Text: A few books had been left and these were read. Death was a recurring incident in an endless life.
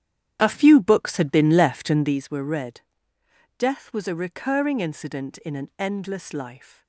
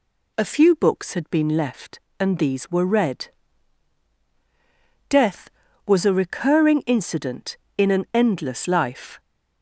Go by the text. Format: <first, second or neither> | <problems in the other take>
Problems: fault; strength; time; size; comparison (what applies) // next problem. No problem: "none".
second | starts louder than the rest; strong; until 2.2 s; 10 dB